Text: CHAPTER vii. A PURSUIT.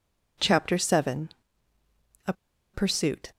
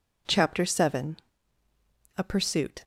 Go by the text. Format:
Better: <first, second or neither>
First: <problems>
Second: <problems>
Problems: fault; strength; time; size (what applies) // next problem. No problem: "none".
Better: second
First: pauses between "A" and "PURSUIT"; at 2.3 s; 0.40 s long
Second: none